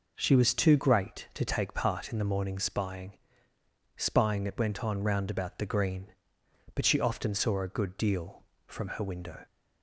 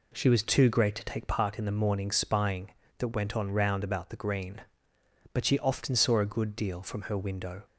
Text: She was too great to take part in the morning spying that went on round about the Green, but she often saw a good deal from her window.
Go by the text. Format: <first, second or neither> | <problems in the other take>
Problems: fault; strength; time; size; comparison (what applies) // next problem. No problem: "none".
second | says "spying" twice; at 3.9 s